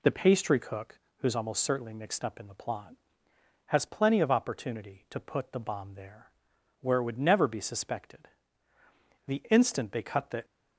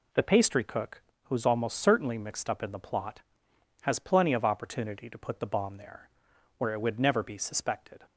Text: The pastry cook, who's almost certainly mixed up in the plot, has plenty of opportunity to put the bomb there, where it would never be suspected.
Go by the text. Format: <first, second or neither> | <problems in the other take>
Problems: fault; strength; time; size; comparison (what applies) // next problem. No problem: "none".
second | goes on to say "The instant they cut the"; noticeable; from 9.2 s on; 1.1 s long